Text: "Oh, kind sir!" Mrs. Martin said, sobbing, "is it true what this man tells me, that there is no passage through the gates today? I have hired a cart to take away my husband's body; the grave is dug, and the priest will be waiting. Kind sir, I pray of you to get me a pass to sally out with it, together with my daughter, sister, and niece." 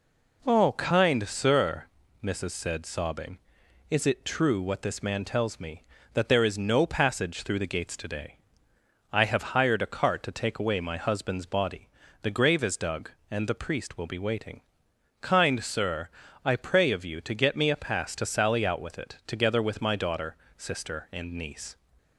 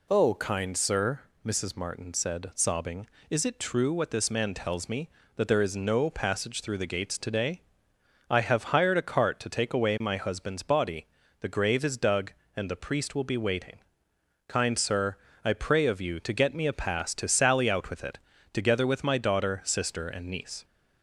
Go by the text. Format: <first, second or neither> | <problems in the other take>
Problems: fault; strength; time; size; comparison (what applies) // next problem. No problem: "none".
second | skips "Martin"; at 2.5 s